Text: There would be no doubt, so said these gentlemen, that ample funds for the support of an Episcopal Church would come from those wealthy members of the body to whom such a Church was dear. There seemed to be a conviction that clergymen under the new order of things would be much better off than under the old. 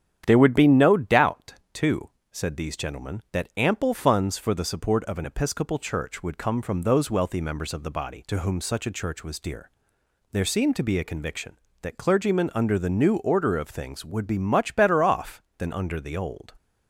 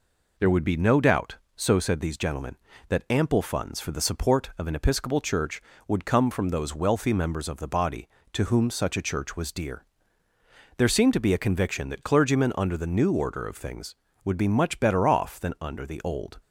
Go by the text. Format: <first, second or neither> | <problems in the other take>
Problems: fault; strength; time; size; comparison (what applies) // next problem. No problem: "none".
second | starts louder than the rest; strong; until 1.2 s; 9.5 dB // says "too" for "so"; at 1.7 s